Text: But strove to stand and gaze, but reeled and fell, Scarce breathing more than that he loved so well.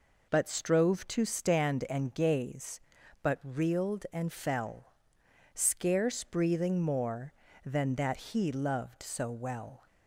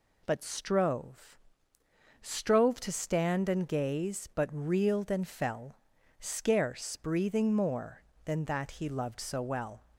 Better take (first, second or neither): first